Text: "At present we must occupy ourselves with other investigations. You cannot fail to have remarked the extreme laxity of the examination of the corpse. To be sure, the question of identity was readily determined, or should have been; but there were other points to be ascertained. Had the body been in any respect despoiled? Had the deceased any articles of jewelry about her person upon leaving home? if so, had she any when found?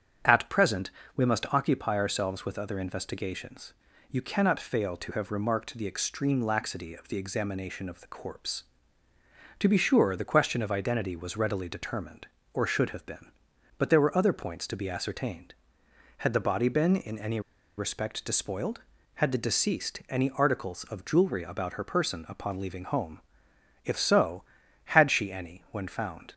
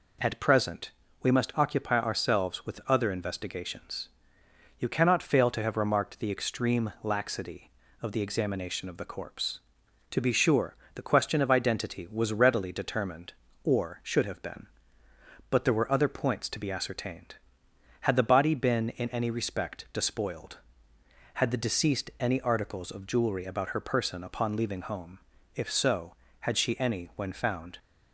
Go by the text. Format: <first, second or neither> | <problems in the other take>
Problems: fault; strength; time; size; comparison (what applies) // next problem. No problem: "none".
second | starts louder than the rest; strong; until 1.4 s; 8.5 dB // pauses between "present" and "we"; slight; at 0.9 s; 0.24 s long; slight in the second // pauses between "any" and "respect"; at 17.3 s; 0.37 s long